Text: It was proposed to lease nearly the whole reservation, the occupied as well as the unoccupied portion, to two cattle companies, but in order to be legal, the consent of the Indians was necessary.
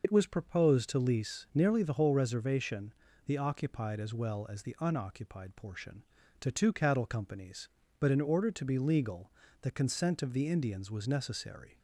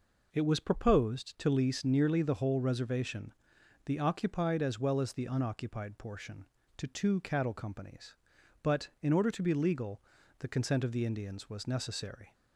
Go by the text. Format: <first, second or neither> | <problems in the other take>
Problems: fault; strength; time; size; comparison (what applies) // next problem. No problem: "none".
second | loses the start of "It"; at 0.0 s; 65 ms